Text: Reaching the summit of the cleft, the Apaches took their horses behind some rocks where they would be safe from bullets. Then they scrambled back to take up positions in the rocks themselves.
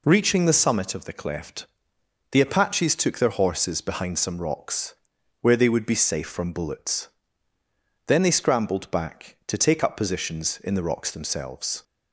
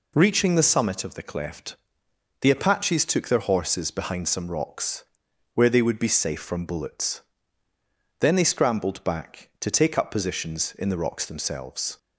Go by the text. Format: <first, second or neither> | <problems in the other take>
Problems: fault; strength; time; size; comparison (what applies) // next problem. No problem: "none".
neither | pauses between "rocks" and "where"; noticeable; the same in both